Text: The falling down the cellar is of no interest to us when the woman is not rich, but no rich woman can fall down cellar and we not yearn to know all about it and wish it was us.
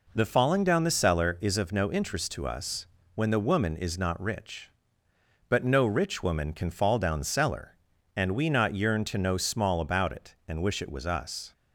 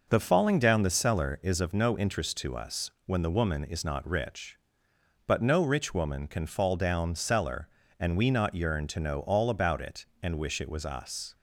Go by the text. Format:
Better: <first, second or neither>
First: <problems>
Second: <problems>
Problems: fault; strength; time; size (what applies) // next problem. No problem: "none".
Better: second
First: pauses between "us" and "when"; slight; at 2.8 s; 0.28 s long // says "small" for "all"; at 9.3 s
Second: pauses between "us" and "when"; slight; at 2.8 s; 0.16 s long